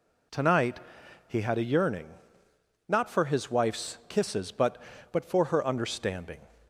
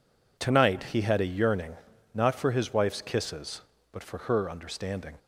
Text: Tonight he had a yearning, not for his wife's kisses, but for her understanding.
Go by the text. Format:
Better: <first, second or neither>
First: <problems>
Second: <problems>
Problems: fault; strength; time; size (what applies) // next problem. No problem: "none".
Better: second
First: pauses between "Tonight" and "he"; noticeable; at 0.7 s; 0.48 s long // says "but" twice; at 5.1 s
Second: none